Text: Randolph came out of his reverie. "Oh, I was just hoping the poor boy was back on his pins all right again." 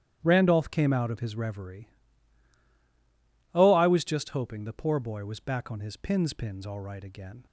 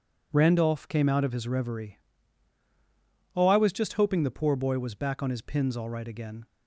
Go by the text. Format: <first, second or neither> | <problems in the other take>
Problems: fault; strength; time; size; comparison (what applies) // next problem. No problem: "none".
second | starts louder than the rest; strong; until 1.2 s; 11.5 dB // says "pins" twice; at 6.3 s